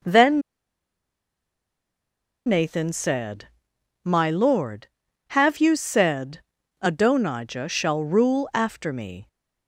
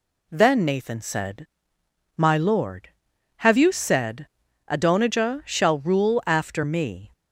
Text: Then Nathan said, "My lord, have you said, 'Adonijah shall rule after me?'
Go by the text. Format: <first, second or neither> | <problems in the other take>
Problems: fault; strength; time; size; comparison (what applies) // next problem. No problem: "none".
second | pauses between "Then" and "Nathan"; strong; at 0.4 s; 2.0 s long